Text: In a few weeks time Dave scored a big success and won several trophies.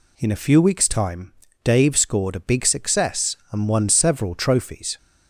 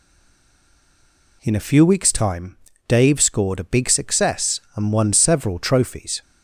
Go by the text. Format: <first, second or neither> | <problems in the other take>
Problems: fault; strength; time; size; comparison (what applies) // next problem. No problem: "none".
first | stays silent before the first word; noticeable; until 1.4 s; 1.4 s long // pauses between "time" and "Dave"; slight; at 2.5 s; 0.32 s long; slight in the first